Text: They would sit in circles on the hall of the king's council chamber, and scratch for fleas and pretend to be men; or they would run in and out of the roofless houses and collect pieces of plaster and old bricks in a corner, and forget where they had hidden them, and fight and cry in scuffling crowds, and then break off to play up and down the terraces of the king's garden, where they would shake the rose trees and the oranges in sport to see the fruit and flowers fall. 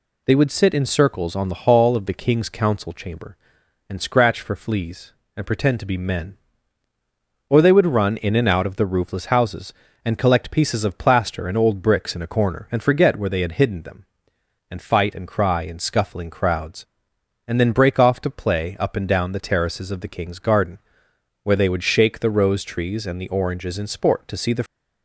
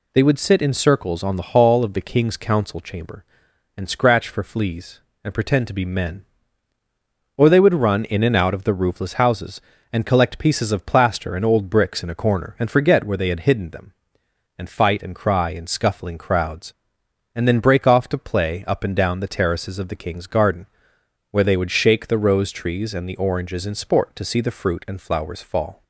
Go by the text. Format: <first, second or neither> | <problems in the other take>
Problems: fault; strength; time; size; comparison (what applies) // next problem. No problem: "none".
second | stops before "fruit and flowers fall"; at 24.6 s